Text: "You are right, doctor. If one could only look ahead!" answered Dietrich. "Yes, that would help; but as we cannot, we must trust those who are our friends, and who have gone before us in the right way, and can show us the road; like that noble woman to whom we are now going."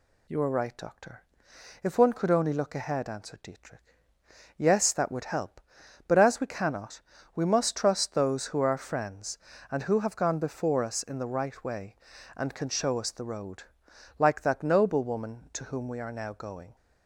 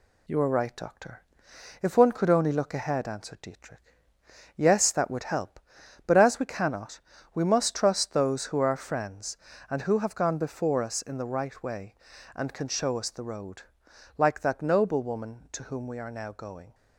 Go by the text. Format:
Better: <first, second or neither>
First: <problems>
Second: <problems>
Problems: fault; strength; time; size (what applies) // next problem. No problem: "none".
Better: first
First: none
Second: gets quieter; slight; throughout; 2.5 dB